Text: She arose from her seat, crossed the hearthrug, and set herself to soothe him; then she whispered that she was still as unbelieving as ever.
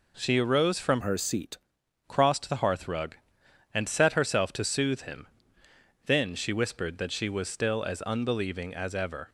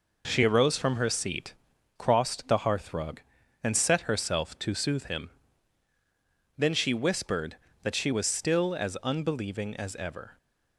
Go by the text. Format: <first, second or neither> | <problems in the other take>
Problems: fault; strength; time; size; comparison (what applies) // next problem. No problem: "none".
second | changes voice from "her" to "seat"; from 1.0 to 1.5 s; 0.5 s long